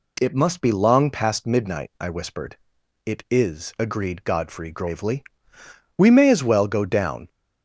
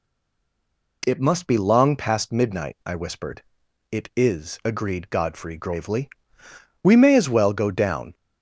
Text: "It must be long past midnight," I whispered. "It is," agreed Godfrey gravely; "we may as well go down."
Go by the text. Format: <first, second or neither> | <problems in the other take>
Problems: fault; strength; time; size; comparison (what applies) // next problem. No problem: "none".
first | stays silent before the first word; until 1.0 s; 1.0 s long